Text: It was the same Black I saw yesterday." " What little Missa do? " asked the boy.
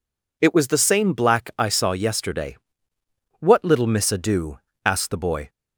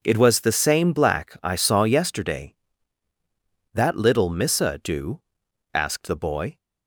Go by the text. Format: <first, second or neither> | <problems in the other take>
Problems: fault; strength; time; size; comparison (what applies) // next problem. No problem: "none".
first | says "That" for "What"; at 3.7 s